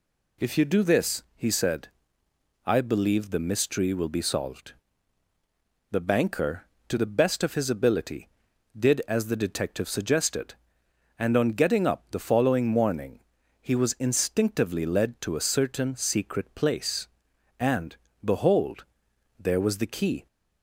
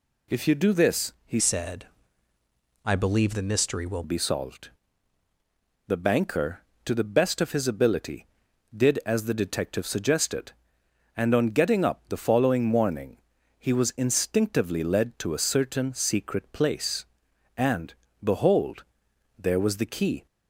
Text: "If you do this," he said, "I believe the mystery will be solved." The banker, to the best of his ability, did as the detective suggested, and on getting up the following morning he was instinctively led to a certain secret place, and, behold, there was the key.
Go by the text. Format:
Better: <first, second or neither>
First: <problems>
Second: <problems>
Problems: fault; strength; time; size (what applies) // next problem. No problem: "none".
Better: first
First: pauses between "morning" and "he"; at 13.2 s; 0.40 s long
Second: changes voice from "said" to "will"; from 1.3 to 4.0 s; 2.7 s long // pauses between "morning" and "he"; at 13.1 s; 0.40 s long